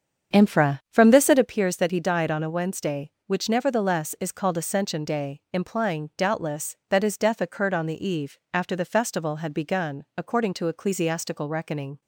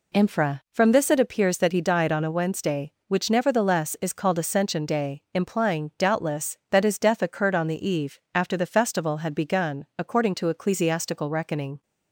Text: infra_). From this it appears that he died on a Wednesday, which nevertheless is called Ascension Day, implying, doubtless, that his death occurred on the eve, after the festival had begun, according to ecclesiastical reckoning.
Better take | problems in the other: second | starts louder than the rest; strong; until 1.6 s; 7.5 dB

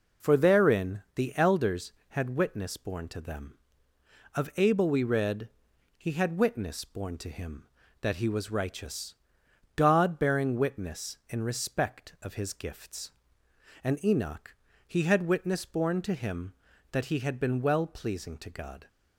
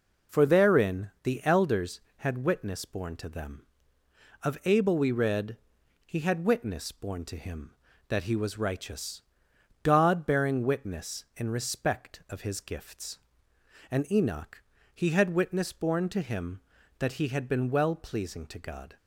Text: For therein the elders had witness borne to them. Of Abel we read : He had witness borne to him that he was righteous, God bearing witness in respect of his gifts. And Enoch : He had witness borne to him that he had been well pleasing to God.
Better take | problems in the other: neither | none

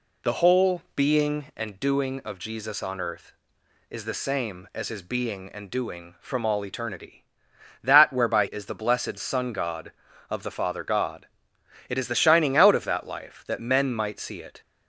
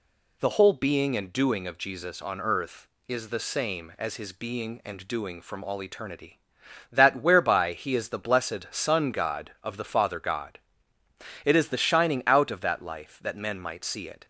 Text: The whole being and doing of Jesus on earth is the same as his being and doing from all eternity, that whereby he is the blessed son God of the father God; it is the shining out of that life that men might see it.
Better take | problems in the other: second | skips "he"; at 8.4 s

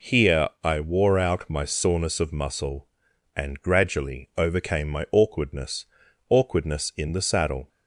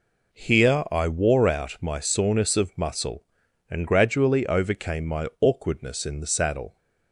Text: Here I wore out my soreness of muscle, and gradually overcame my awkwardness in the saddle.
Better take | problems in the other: second | pauses between "Here" and "I"; slight; at 0.4 s; 0.16 s long // says "awkwardness" twice; at 6.3 s

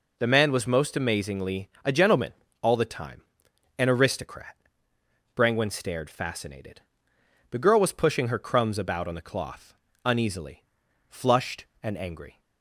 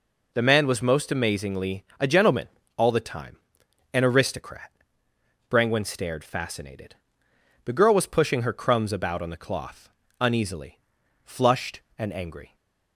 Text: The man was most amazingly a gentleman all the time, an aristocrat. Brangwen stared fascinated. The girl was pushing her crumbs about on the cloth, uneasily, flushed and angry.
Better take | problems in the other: neither | pauses between "amazingly" and "a"; slight; the same in both // pauses between "gentleman" and "all"; slight; the same in both

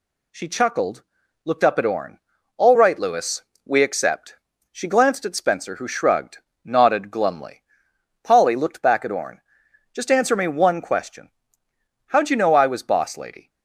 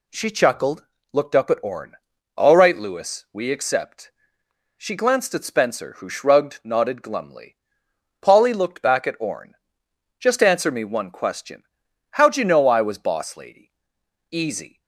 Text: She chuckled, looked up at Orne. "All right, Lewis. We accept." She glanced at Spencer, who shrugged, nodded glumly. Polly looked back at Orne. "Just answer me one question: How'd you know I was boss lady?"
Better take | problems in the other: first | goes on to say "Easy"; from 14.2 s on; 0.52 s long

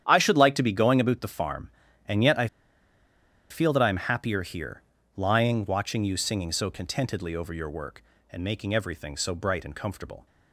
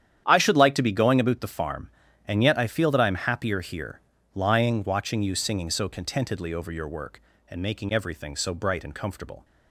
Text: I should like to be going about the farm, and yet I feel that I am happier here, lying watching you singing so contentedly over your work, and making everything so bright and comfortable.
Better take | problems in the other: second | starts louder than the rest; strong; until 1.0 s; 10 dB; strong in the second // pauses between "I" and "feel"; at 2.4 s; 1.0 s long

